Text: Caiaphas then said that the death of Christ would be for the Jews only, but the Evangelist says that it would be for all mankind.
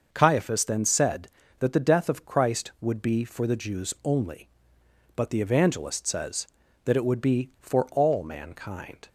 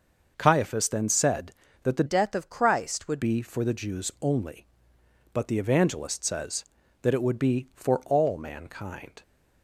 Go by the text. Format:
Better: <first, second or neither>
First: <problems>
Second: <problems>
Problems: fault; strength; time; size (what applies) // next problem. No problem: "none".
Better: first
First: starts louder than the rest; noticeable; until 1.1 s; 6 dB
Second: starts louder than the rest; noticeable; until 1.3 s; 6 dB // changes voice from "death" to "would"; from 2.0 to 3.2 s; 1.2 s long